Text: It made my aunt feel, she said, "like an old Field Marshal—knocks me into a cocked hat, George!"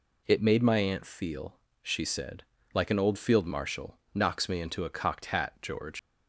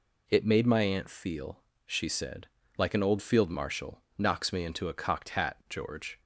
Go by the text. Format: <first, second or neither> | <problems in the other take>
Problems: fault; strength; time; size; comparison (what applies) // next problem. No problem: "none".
second | leaves "George" unfinished; at 5.9 s; 130 ms